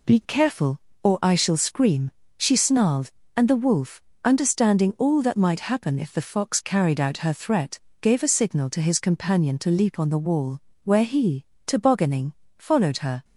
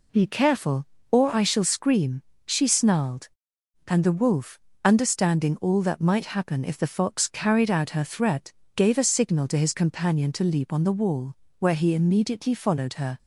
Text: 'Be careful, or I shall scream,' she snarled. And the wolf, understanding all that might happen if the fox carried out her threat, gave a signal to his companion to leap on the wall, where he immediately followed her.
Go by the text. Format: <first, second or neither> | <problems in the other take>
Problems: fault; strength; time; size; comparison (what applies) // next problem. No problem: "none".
second | says "tobogganing" for "immediately"; at 11.6 s